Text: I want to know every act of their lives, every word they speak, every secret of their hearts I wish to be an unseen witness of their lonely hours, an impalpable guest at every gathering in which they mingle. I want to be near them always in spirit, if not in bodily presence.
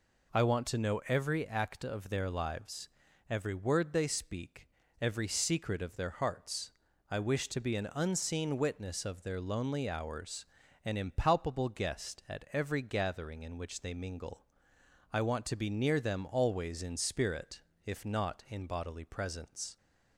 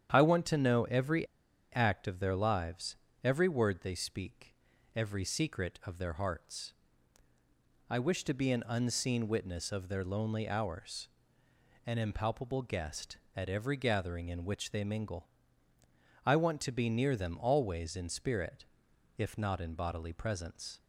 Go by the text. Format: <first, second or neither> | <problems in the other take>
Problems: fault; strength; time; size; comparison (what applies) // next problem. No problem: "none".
first | starts louder than the rest; strong; until 1.1 s; 9 dB // pauses between "every" and "act"; noticeable; at 1.2 s; 0.48 s long // pauses between "hearts" and "I"; at 6.7 s; 1.1 s long; also in the first